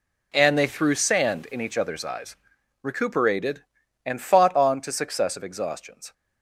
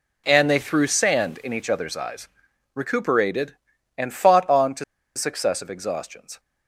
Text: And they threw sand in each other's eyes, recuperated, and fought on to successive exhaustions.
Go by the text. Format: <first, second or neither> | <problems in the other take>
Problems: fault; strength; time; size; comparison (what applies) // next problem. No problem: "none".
first | pauses between "to" and "successive"; slight; at 4.8 s; 0.33 s long